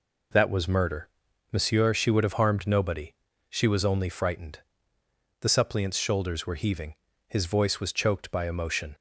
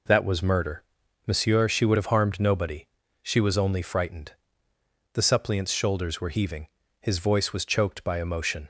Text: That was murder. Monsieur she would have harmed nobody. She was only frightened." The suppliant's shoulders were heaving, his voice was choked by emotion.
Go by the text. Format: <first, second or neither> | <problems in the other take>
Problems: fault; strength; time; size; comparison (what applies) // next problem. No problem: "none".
neither | none